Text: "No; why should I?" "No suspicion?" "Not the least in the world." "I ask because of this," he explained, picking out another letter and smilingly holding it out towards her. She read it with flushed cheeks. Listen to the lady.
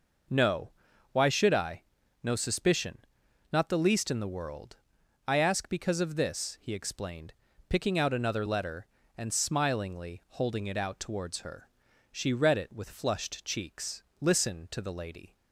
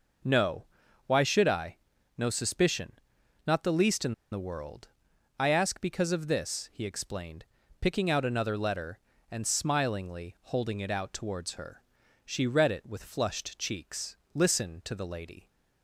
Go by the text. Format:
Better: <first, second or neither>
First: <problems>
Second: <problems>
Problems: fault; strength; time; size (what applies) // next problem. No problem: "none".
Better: first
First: none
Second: pauses between "in" and "the"; slight; at 4.1 s; 0.19 s long